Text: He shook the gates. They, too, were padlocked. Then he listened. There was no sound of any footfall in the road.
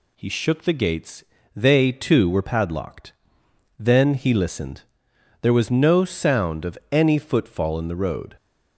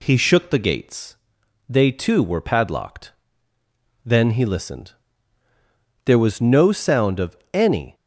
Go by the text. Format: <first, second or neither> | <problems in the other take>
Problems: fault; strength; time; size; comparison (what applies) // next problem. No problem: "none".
first | pauses between "of" and "any"; slight; at 7.3 s; 0.18 s long // stops before "footfall in the road"; at 7.9 s